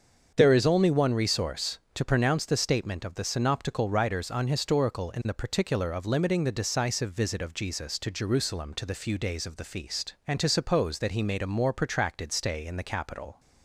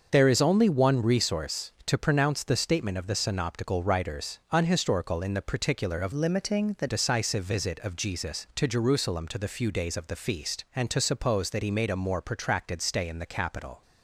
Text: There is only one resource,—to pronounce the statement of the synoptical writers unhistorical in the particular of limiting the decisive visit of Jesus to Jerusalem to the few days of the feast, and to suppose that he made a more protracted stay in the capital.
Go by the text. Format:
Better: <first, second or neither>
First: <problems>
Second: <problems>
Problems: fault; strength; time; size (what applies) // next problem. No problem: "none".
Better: first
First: starts louder than the rest; until 1.3 s; 7 dB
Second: starts louder than the rest; until 1.1 s; 6.5 dB // changes voice from "limiting" to "the"; from 6.1 to 6.8 s; 0.7 s long